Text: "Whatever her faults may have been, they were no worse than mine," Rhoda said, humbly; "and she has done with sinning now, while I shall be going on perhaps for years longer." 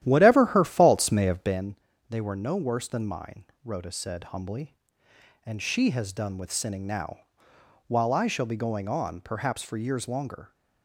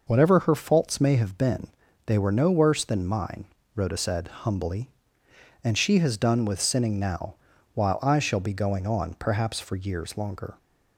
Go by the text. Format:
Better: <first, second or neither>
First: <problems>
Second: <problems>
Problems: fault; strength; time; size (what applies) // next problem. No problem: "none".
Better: second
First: starts louder than the rest; strong; until 1.7 s; 12 dB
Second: none